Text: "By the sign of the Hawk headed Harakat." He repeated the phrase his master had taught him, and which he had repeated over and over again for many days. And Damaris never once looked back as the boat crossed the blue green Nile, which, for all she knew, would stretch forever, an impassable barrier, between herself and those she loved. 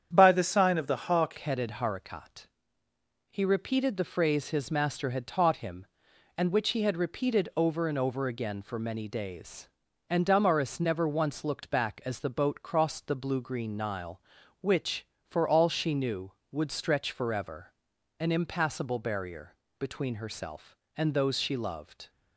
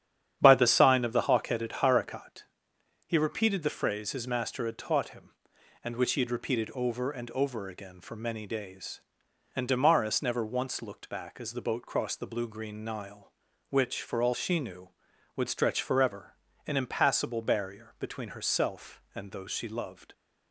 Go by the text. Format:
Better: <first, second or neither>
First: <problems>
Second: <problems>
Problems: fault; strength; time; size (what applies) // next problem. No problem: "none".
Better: second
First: starts louder than the rest; strong; until 1.1 s; 8.5 dB // changes voice at "headed"; from 1.3 s on; 20.7 s long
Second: starts louder than the rest; strong; until 1.4 s; 9.5 dB